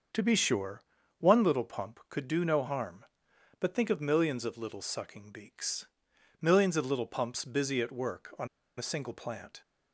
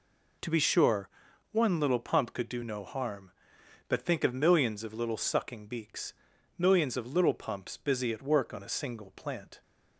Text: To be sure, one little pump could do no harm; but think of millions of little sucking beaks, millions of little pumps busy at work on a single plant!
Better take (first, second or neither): second